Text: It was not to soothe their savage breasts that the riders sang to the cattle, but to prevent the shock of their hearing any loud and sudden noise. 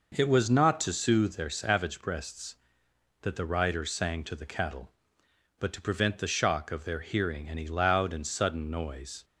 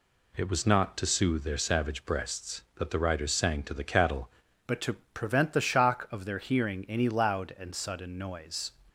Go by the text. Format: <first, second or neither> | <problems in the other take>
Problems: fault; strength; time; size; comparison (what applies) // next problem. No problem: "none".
first | changes voice at "but"; from 4.6 s on; 4.1 s long // pauses between "to" and "prevent"; slight; at 4.9 s; 0.18 s long